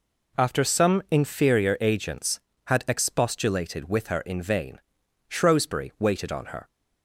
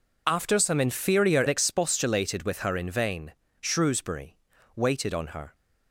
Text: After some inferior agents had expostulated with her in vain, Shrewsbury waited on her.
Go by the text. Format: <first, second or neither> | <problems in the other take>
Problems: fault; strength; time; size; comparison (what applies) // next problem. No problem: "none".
first | skips "agents had"; at 1.4 s // pauses between "Shrewsbury" and "waited"; at 4.3 s; 0.38 s long